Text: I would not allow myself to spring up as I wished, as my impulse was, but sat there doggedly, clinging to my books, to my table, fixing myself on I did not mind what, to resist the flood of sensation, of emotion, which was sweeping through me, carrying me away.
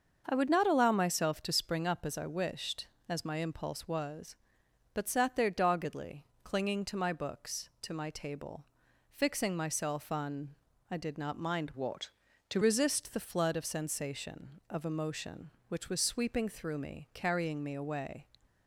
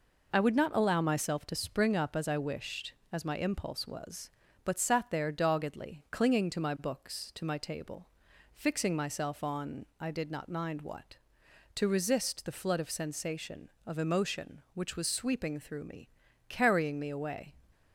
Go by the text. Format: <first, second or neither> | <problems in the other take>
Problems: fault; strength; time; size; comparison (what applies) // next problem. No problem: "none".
second | starts louder than the rest; until 1.2 s; 6.5 dB // pauses between "on" and "I"; slight; at 10.5 s; 0.34 s long // changes voice from "what" to "to"; from 11.7 to 12.6 s; 0.9 s long